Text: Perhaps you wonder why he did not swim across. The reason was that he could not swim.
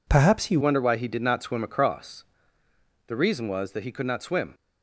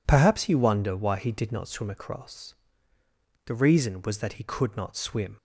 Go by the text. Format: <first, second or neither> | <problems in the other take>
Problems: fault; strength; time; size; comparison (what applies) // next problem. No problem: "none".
second | changes voice at "wonder"; from 0.6 s on; 3.9 s long